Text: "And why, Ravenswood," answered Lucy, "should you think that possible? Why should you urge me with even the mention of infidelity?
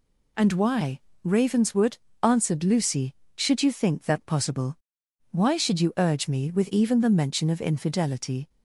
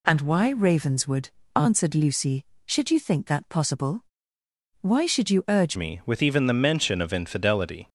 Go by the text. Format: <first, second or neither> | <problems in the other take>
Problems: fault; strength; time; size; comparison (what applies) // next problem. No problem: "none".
first | changes voice at "me"; from 5.7 s on; 2.1 s long